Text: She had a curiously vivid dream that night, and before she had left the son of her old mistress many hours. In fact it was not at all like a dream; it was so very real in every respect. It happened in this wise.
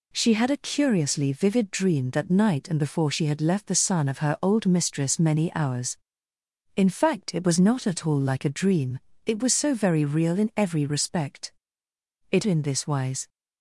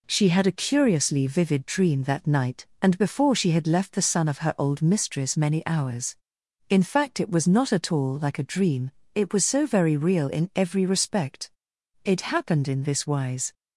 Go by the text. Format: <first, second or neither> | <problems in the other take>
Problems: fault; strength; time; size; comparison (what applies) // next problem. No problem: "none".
second | skips "happened"; at 12.4 s